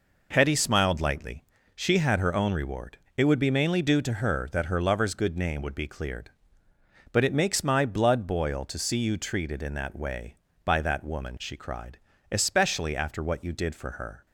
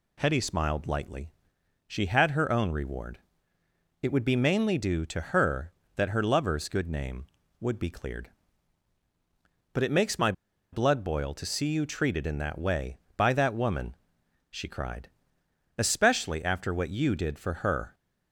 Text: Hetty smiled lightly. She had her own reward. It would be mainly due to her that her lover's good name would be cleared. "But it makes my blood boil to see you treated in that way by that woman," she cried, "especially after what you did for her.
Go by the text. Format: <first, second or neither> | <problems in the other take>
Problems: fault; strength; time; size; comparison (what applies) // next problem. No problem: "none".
first | pauses between "my" and "blood"; at 10.3 s; 0.39 s long